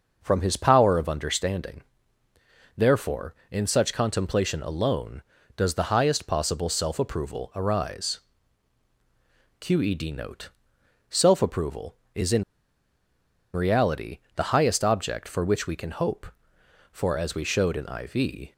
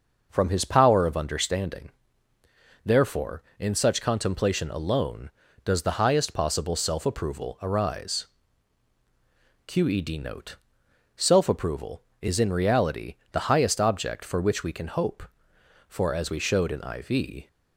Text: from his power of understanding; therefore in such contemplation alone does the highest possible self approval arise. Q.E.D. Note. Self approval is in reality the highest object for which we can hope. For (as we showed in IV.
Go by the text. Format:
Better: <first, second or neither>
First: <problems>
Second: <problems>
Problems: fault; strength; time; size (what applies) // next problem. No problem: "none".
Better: second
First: pauses between "in" and "reality"; at 12.4 s; 1.1 s long // pauses between "reality" and "the"; slight; at 14.1 s; 0.16 s long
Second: pauses between "reality" and "the"; slight; at 13.1 s; 0.16 s long